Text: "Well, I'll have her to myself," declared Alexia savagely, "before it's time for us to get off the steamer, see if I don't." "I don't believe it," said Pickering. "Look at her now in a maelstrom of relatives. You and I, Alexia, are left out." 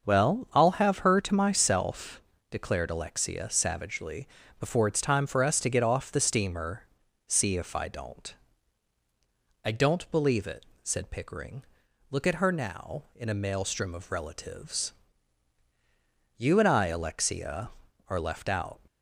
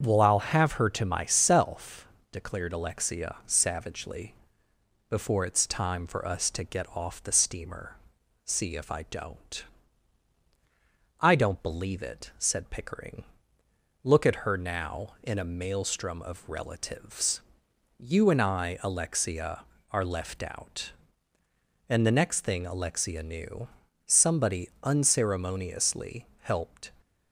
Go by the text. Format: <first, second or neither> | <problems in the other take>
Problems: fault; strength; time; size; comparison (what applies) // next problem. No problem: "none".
first | starts louder than the rest; until 1.0 s; 7 dB // goes on to say "And the next thing Alexia knew somebody unceremoniously helped"; strong; from 21.8 s on; 5.0 s long